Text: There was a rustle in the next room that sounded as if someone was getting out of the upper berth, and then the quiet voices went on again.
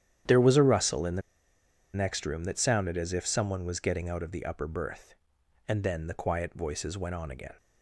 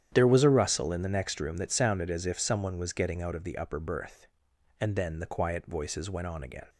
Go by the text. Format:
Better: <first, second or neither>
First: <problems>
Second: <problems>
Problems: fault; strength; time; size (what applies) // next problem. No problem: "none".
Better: second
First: starts louder than the rest; strong; until 2.0 s; 10 dB // pauses between "the" and "next"; noticeable; at 1.2 s; 0.73 s long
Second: starts louder than the rest; strong; until 1.1 s; 10 dB